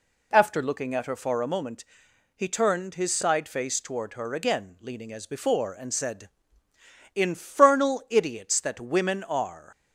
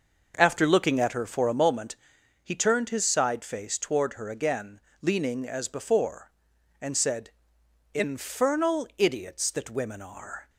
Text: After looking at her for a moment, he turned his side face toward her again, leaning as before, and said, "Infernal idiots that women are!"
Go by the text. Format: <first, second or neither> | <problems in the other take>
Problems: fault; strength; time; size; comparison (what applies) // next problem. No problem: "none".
first | starts louder than the rest; noticeable; until 1.6 s; 6 dB